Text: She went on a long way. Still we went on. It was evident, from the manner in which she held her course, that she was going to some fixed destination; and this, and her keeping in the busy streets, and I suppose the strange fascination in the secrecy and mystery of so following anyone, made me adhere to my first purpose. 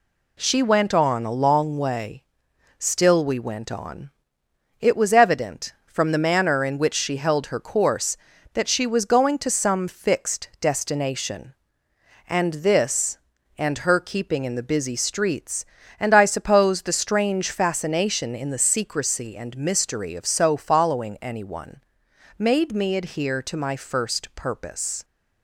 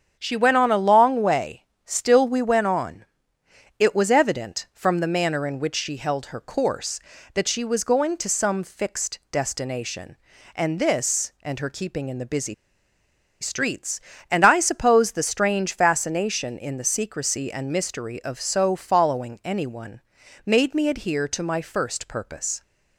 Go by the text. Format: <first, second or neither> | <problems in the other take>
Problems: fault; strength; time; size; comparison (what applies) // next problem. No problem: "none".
first | starts louder than the rest; strong; until 1.2 s; 7.5 dB // pauses between "busy" and "streets"; noticeable; at 12.5 s; 0.87 s long